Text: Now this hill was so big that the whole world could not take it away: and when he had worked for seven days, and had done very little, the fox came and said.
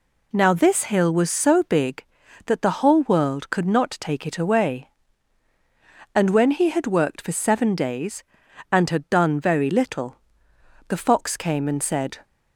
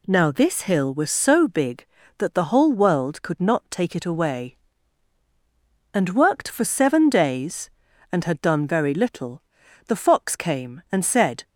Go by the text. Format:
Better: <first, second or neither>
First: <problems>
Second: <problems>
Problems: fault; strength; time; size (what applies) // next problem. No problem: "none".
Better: first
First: none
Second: skips "when he had"; at 6.1 s